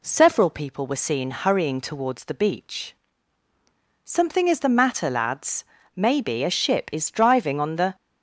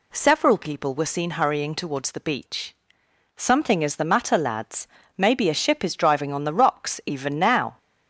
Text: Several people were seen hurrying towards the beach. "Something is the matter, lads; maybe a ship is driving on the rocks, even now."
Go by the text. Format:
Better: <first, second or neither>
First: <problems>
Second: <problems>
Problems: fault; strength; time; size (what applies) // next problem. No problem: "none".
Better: second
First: stops before "rocks even now"; at 7.9 s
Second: none